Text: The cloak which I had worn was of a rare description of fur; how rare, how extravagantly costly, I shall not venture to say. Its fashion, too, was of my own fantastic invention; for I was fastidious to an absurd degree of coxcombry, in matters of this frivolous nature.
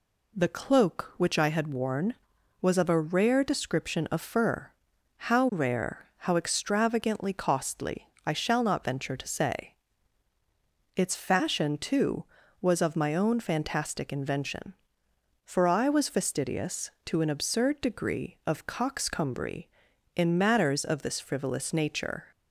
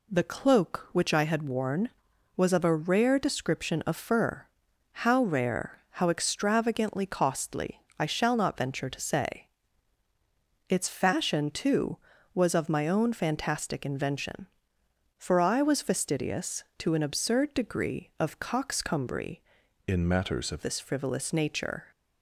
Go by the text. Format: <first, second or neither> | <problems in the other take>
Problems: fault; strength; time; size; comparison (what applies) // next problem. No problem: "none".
first | changes voice from "in" to "of"; from 19.8 to 20.6 s; 0.8 s long